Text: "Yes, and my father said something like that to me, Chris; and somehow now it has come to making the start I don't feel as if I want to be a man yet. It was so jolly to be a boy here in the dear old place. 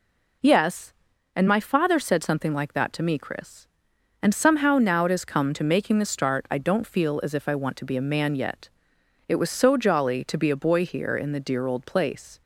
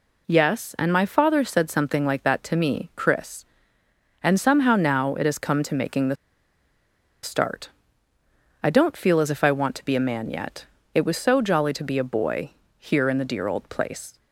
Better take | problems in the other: first | pauses between "the" and "start"; at 6.1 s; 1.0 s long // pauses between "start" and "I"; noticeable; at 7.7 s; 0.92 s long // pauses between "boy" and "here"; slight; at 12.5 s; 0.28 s long

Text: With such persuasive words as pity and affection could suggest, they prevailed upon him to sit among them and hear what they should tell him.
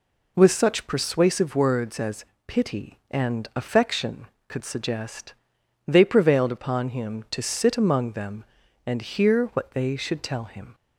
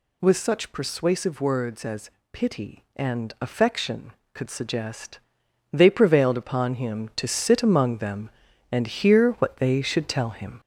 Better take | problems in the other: first | gets louder; throughout; 3.5 dB // pauses between "as" and "pity"; slight; at 2.0 s; 0.22 s long; slight in the first

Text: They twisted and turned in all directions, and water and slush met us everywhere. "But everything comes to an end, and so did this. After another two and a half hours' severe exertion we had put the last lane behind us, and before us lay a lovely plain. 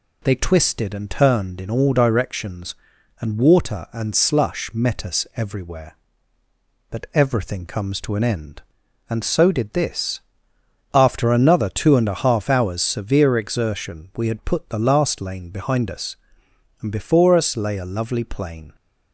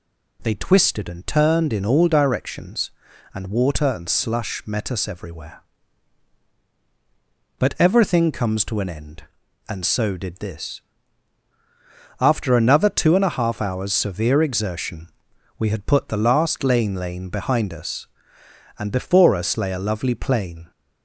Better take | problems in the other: first | pauses between "exertion" and "we"; noticeable; at 15.0 s; 0.50 s long // says "lane" twice; at 16.9 s

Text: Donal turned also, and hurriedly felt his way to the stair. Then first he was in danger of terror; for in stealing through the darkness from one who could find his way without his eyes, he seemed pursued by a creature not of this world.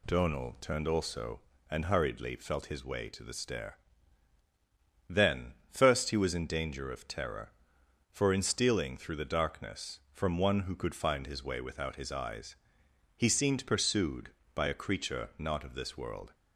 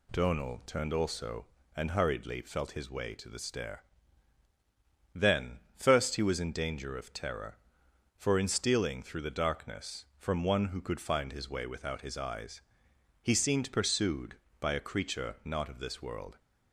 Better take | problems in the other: neither | pauses between "Then" and "first"; slight; the same in both

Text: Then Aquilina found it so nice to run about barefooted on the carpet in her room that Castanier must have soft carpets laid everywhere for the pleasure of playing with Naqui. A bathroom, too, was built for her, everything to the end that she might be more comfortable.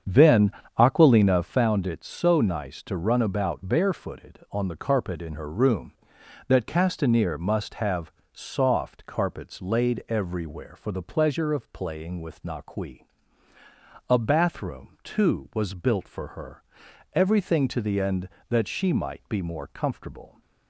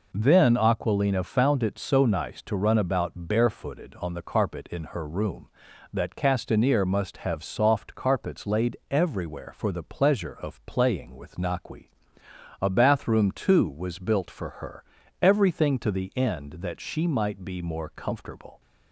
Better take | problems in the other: second | starts louder than the rest; strong; until 1.7 s; 7.5 dB // pauses between "Then" and "Aquilina"; slight; at 0.5 s; 0.28 s long // pauses between "have" and "soft"; slight; at 8.1 s; 0.22 s long

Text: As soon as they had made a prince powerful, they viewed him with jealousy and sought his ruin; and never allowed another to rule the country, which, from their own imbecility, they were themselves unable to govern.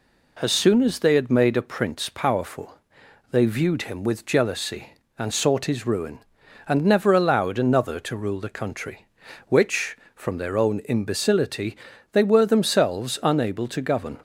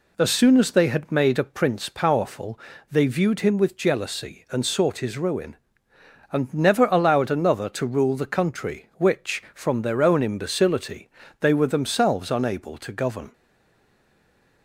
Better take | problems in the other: first | stays silent after the last word; noticeable; from 13.3 s on; 1.3 s long

